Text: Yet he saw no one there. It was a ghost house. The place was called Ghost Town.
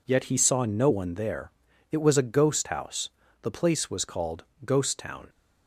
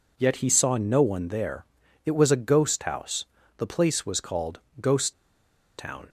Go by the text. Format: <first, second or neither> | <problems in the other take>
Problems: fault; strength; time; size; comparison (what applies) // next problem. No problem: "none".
first | pauses between "called" and "Ghost"; slight; at 4.6 s; 0.20 s long; slight in the first // pauses between "Ghost" and "Town"; noticeable; at 5.1 s; 0.64 s long